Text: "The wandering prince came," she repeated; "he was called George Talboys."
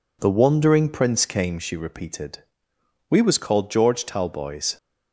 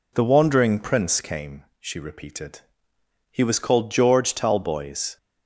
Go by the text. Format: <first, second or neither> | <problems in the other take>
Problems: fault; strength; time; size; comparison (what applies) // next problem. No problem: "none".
second | says "we" for "he"; at 3.0 s